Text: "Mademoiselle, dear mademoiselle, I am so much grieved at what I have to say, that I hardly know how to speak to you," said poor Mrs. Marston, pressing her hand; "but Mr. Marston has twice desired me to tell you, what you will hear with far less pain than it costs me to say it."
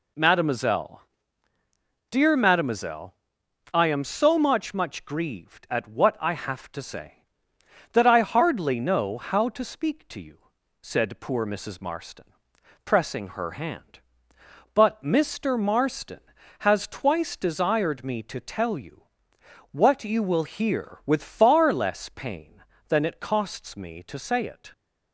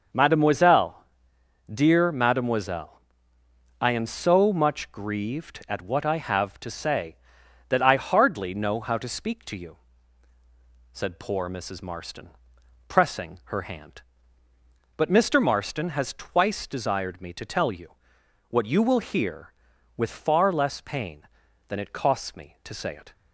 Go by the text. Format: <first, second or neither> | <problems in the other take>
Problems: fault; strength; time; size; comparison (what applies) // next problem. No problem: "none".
second | says "much" twice; at 4.7 s